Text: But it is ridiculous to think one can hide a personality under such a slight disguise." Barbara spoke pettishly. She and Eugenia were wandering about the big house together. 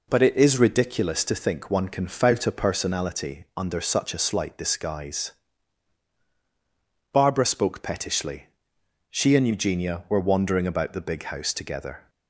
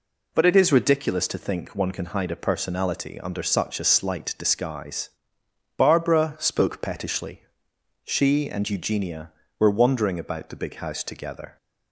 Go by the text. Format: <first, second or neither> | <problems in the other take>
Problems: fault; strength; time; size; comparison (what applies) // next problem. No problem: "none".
second | says "fout" for "hide"; at 2.0 s